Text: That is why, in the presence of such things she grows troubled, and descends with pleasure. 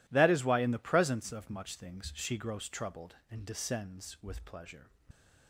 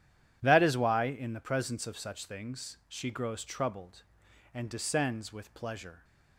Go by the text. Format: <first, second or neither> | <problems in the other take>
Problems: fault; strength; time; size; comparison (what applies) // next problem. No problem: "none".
second | says "much" for "such"; at 1.4 s